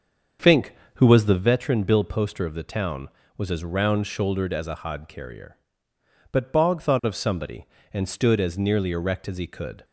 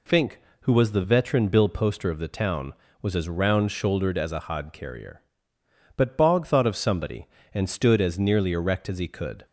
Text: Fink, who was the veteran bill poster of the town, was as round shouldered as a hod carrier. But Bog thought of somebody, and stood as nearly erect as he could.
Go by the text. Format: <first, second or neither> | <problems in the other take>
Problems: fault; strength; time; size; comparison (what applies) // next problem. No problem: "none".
second | starts louder than the rest; until 1.5 s; 7 dB